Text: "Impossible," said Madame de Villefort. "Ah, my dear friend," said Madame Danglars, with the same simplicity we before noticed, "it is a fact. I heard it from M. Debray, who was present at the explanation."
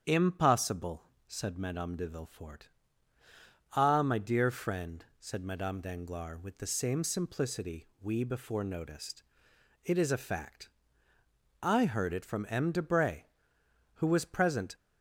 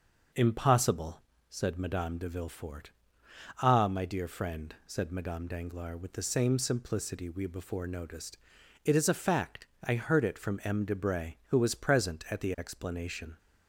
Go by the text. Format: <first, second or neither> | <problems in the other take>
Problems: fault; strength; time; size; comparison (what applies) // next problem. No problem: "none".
second | starts louder than the rest; strong; until 1.3 s; 8 dB; noticeable in the second // stops before "at the explanation"; at 14.7 s